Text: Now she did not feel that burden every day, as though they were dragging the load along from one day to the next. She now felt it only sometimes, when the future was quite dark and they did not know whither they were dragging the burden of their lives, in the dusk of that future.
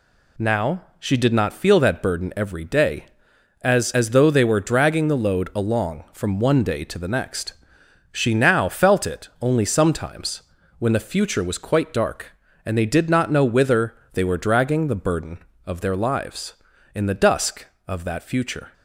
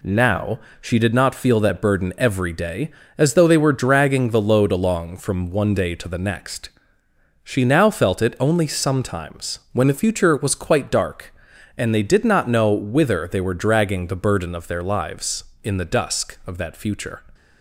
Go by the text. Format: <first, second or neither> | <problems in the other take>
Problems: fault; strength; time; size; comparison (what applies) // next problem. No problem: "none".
second | pauses between "Now" and "she"; slight; at 0.8 s; 0.16 s long; slight in the second // says "as" twice; at 3.9 s // pauses between "whither" and "they"; slight; at 13.9 s; 0.18 s long